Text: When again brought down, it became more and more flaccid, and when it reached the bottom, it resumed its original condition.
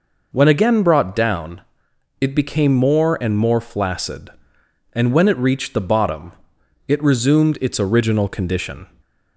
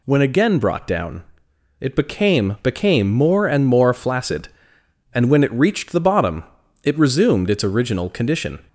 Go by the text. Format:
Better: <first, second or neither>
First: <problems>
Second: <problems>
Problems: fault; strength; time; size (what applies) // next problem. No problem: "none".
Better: first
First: none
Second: says "became" twice; at 2.6 s